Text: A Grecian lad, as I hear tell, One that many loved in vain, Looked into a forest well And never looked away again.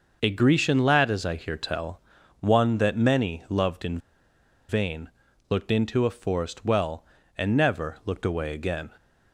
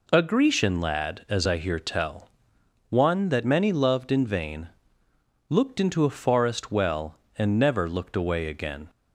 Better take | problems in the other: second | starts louder than the rest; noticeable; until 1.2 s; 6 dB // pauses between "in" and "vain"; noticeable; at 3.9 s; 0.71 s long

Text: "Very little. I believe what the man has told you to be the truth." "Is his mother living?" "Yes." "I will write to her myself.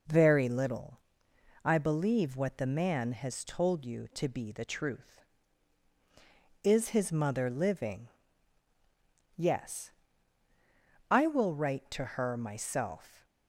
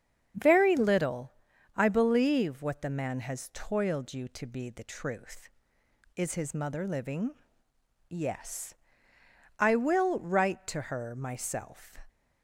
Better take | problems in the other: first | starts louder than the rest; strong; until 1.8 s; 8 dB // says "toiled" for "told"; at 3.5 s

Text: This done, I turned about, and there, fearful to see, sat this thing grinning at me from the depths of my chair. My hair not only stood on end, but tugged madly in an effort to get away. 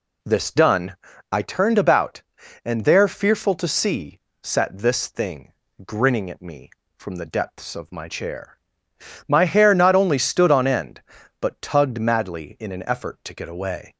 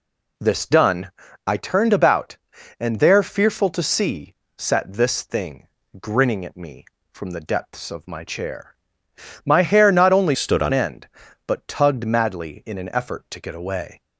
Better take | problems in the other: first | pauses between "thing" and "grinning"; slight; at 5.6 s; 0.36 s long; slight in the first // changes voice from "stood" to "on"; from 10.3 to 10.7 s; 0.4 s long

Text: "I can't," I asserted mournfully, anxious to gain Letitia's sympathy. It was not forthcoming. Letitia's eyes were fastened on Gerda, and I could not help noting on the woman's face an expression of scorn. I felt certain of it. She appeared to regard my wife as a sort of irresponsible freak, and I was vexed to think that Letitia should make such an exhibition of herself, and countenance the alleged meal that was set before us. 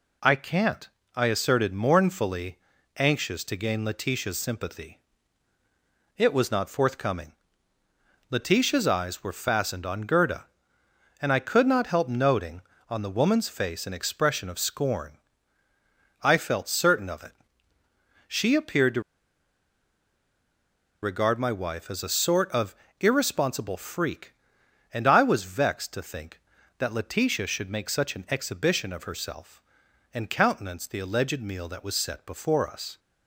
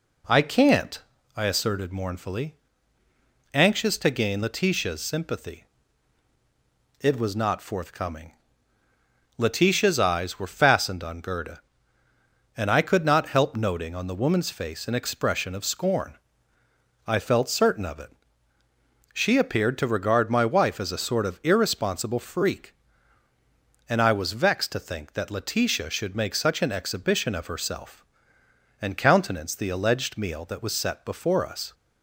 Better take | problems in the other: second | pauses between "to" and "regard"; strong; at 19.0 s; 2.0 s long // pauses between "of" and "irresponsible"; slight; at 22.7 s; 0.26 s long

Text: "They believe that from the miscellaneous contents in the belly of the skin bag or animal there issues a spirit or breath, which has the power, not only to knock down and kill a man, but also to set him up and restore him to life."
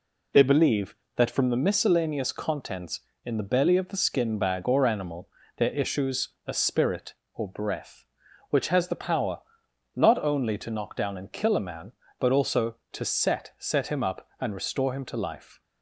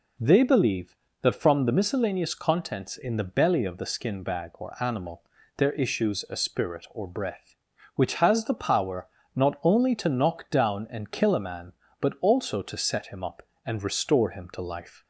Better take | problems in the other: second | pauses between "animal" and "there"; slight; at 5.2 s; 0.28 s long; slight in the second // pauses between "issues" and "a"; slight; at 6.2 s; 0.18 s long // says "set" twice; at 13.5 s

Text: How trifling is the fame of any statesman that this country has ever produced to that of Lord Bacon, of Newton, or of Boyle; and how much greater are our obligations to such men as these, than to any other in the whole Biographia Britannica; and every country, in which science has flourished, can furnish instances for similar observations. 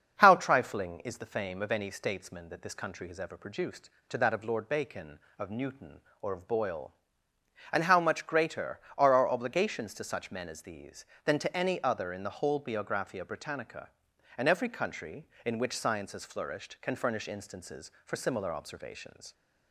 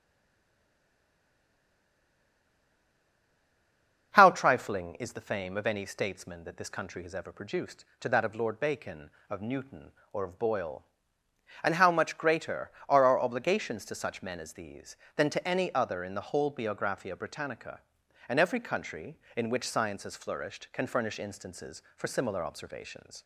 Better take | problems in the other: first | stays silent before the first word; strong; until 4.1 s; 4.1 s long // starts louder than the rest; until 5.1 s; 7 dB; also in the first

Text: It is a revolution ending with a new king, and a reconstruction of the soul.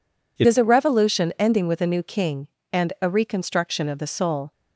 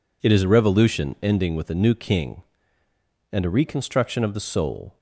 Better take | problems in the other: second | changes voice at "is"; from 0.4 s on; 4.1 s long

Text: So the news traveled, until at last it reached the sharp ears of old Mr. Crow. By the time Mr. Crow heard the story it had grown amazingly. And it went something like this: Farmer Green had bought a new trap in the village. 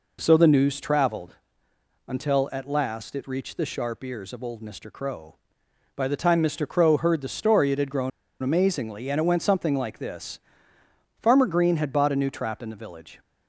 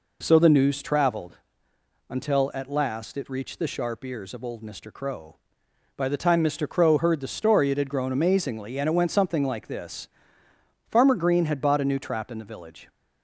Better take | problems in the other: second | pauses between "grown" and "amazingly"; slight; at 8.1 s; 0.31 s long

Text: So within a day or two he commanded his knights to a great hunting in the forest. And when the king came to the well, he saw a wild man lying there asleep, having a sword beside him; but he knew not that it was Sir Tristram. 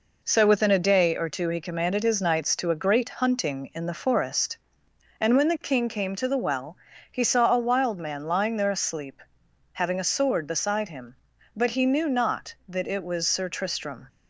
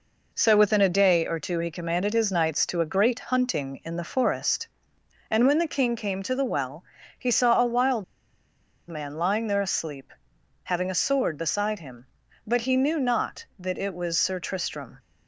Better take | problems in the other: first | pauses between "wild" and "man"; noticeable; at 8.0 s; 0.85 s long

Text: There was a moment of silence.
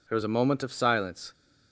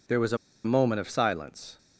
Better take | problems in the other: first | pauses between "a" and "moment"; slight; at 0.3 s; 0.28 s long

